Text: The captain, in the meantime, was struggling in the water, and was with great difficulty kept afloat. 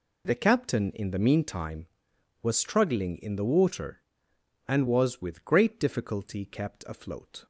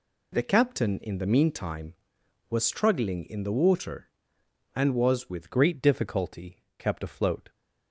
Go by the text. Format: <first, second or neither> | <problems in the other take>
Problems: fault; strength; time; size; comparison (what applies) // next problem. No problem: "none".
first | changes voice at "great"; from 5.5 s on; 2.0 s long // pauses between "difficulty" and "kept"; slight; at 6.6 s; 0.16 s long